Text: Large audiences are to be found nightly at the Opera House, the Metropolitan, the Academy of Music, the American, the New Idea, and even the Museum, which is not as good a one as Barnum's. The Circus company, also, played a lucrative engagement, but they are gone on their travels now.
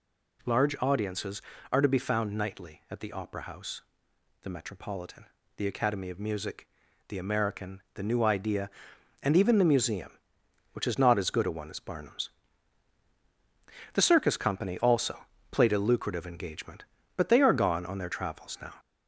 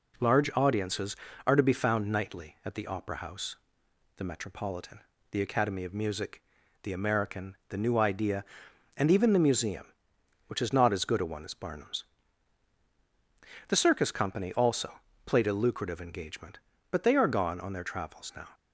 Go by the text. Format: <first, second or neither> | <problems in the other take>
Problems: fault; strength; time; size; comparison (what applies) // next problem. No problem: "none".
second | gets louder; slight; throughout; 3 dB